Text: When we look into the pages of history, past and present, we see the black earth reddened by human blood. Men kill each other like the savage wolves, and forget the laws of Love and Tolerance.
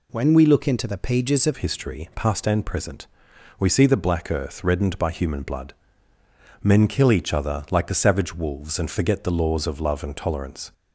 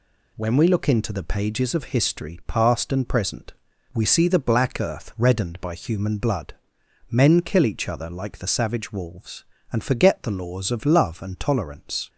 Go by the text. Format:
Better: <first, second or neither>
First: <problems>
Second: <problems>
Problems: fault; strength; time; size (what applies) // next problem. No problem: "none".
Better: second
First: changes voice at "history"; from 1.5 s on; 9.2 s long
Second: none